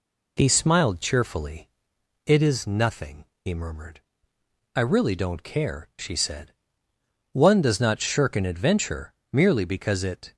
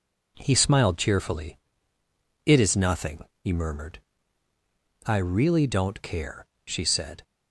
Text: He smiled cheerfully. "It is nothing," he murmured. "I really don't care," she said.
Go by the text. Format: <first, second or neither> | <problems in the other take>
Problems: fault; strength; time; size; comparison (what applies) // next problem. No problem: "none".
second | goes on to say "One does not shirk an adventure merely because it"; strong; from 7.3 s on; 3.0 s long